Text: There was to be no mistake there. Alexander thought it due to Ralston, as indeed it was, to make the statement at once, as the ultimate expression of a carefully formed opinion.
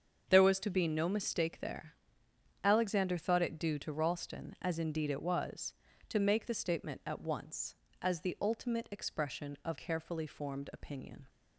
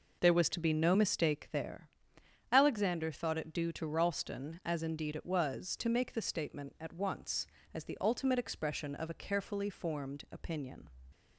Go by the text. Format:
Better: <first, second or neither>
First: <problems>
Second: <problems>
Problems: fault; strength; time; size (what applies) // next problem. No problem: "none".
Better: second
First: starts louder than the rest; until 1.3 s; 7 dB // skips "a"; at 9.7 s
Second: none